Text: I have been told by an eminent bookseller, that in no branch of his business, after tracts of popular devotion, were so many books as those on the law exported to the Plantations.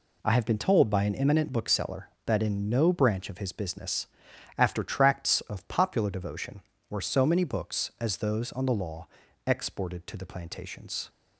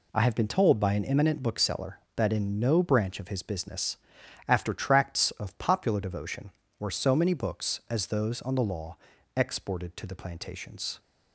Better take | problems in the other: neither | pauses between "law" and "exported"; the same in both

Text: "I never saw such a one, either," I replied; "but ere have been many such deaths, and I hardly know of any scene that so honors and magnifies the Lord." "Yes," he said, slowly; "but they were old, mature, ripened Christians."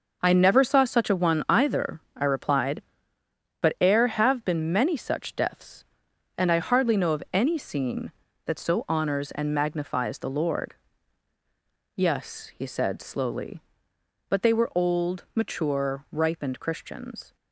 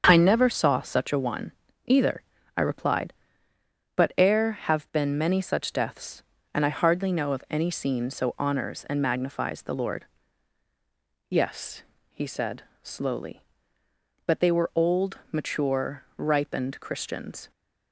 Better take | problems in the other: first | starts louder than the rest; until 1.0 s; 7 dB // skips "that"; at 8.0 s

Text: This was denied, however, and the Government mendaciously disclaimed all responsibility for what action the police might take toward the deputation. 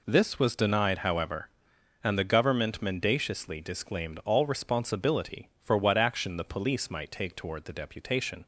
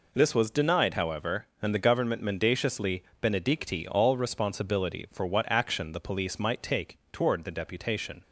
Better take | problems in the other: first | says "benedicti" for "disclaimed"; at 3.2 s // pauses between "take" and "toward"; slight; at 6.9 s; 0.16 s long

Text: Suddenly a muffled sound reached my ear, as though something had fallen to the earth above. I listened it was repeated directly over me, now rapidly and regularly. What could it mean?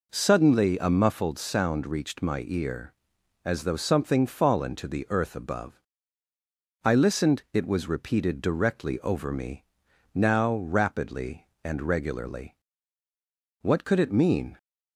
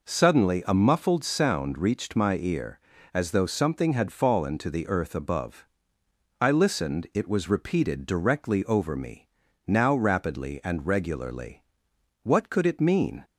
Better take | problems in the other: second | skips "had"; at 4.2 s

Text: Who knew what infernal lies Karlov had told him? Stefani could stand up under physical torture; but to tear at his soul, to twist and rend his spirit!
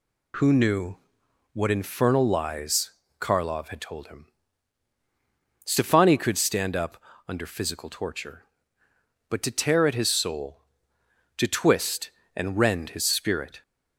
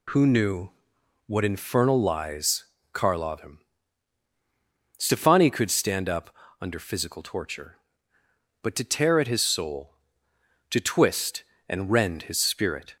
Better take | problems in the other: first | pauses between "knew" and "what"; noticeable; at 0.7 s; 0.56 s long; noticeable in the first // pauses between "lies" and "Karlov"; slight; at 2.6 s; 0.30 s long; slight in the first // skips "had told"; at 3.3 s // pauses between "up" and "under"; slight; at 6.2 s; 0.28 s long; slight in the first

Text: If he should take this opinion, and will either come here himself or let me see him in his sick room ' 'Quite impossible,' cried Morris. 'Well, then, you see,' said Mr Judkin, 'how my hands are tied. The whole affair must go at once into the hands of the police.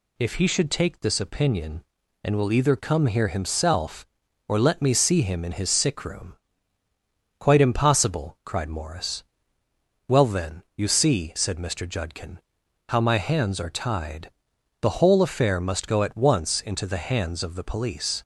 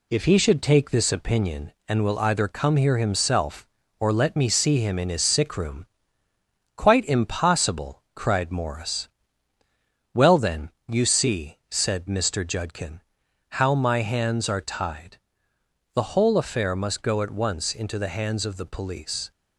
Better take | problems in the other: first | gets quieter; slight; throughout; 2 dB

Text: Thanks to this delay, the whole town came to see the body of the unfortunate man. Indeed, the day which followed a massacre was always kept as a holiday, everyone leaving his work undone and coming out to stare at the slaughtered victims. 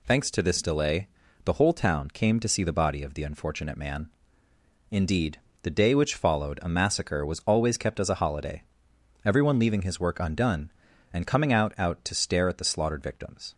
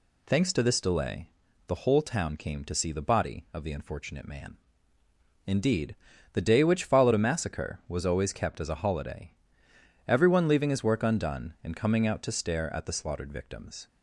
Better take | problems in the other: second | says "out" twice; at 11.7 s

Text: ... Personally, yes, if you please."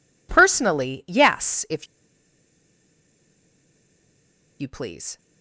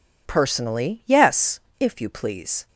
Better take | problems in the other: second | pauses between "if" and "you"; strong; at 1.8 s; 2.7 s long

